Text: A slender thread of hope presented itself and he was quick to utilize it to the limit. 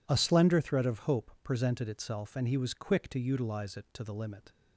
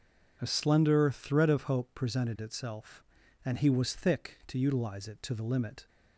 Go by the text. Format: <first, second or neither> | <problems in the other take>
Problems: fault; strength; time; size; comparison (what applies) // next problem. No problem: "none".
first | says "thick" for "quick"; at 3.9 s